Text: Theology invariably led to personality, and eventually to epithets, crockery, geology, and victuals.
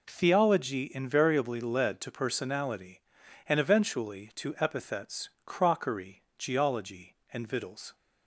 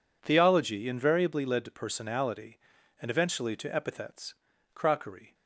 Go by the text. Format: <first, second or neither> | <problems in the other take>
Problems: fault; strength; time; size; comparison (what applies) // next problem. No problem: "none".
first | stops before "geology and victuals"; at 5.3 s